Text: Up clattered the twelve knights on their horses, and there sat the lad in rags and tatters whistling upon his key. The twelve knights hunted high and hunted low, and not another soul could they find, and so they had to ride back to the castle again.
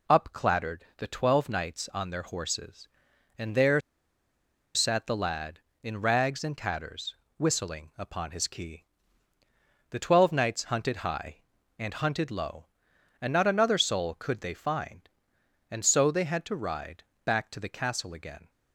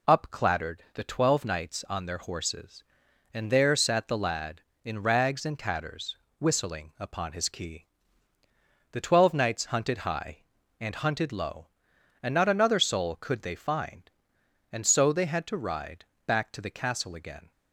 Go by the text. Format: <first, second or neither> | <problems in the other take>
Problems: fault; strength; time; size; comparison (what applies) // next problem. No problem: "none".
second | pauses between "there" and "sat"; noticeable; at 3.7 s; 0.95 s long // pauses between "tatters" and "whistling"; slight; at 7.1 s; 0.22 s long; slight in the second // pauses between "ride" and "back"; slight; at 17.0 s; 0.20 s long; slight in the second